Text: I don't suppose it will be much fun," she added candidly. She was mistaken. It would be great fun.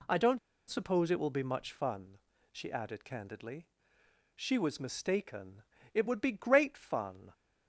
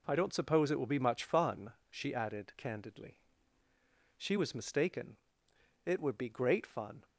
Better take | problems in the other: second | pauses between "don't" and "suppose"; slight; at 0.3 s; 0.31 s long

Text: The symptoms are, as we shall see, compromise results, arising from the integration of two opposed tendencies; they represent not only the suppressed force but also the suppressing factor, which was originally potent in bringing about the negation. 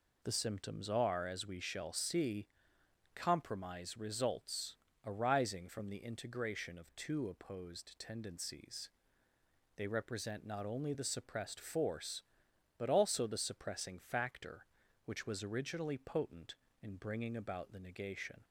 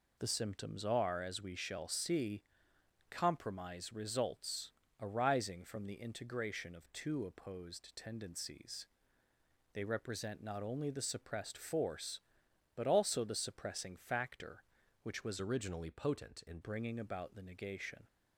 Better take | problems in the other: first | changes voice from "originally" to "in"; from 15.4 to 16.6 s; 1.2 s long

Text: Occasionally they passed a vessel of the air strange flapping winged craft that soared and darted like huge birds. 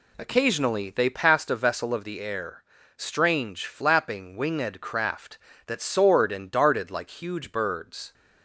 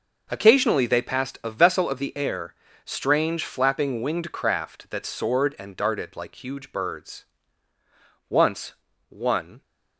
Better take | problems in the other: first | pauses between "air" and "strange"; slight; at 2.5 s; 0.30 s long; slight in the first // goes on to say "Once one"; from 8.2 s on; 1.3 s long

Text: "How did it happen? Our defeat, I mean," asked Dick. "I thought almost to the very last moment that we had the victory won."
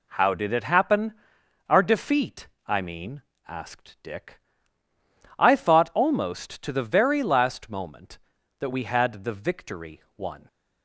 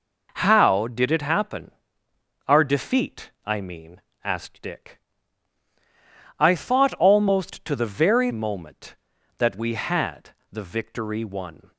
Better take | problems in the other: first | skips "last"; at 8.3 s // pauses between "had" and "the"; slight; at 10.2 s; 0.22 s long

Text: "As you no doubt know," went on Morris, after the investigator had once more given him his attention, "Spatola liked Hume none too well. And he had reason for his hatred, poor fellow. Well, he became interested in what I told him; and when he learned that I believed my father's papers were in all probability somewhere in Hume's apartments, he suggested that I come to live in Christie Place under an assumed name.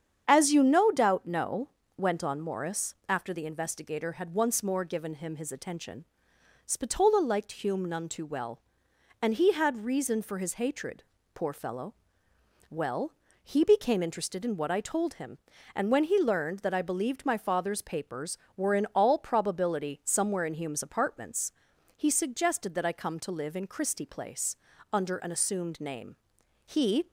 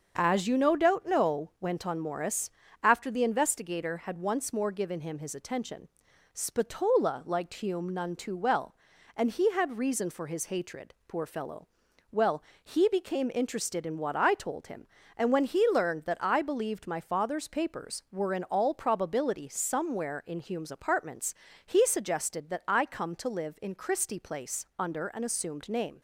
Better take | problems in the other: second | starts louder than the rest; strong; until 1.2 s; 8 dB; also in the second // pauses between "Place" and "under"; slight; at 24.5 s; 0.34 s long // goes on to say "He"; slight; from 26.6 s on; 0.46 s long

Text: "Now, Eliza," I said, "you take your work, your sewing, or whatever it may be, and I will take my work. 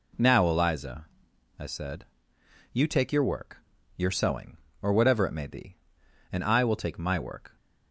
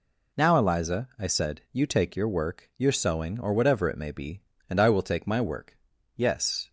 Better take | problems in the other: first | goes on to say "Yes"; from 6.1 s on; 0.54 s long

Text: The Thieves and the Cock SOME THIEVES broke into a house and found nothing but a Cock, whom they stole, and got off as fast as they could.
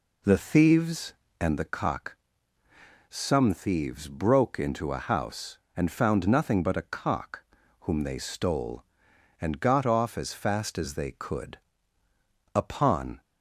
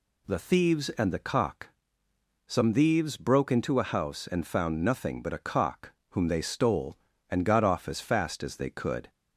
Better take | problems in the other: second | pauses between "Cock" and "SOME"; noticeable; at 2.1 s; 0.92 s long; noticeable in the second // goes on to say "Upon"; noticeable; from 12.5 s on; 0.66 s long

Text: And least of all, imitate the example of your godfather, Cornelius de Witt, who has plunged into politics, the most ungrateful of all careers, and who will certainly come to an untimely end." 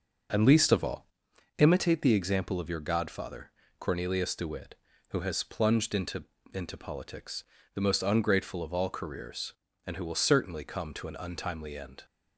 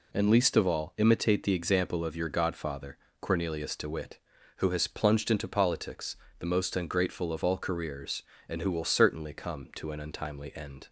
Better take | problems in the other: second | says "into" twice; at 6.5 s

